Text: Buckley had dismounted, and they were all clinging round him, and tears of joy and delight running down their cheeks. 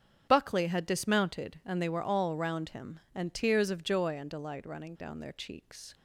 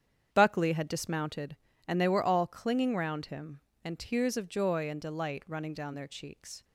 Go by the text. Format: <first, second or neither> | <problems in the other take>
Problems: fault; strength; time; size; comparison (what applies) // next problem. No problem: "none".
second | starts louder than the rest; strong; until 1.3 s; 8 dB; strong in the second // skips "clinging"; at 2.3 s